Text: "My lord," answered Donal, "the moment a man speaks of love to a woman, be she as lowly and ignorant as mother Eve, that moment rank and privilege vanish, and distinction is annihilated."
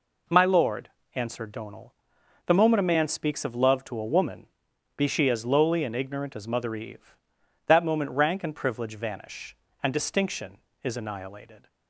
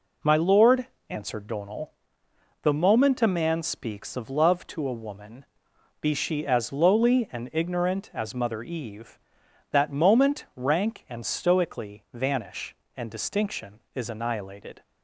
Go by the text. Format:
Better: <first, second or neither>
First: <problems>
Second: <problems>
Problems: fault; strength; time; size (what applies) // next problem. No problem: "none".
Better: first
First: none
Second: says "stoically" for "privilege"; at 11.2 s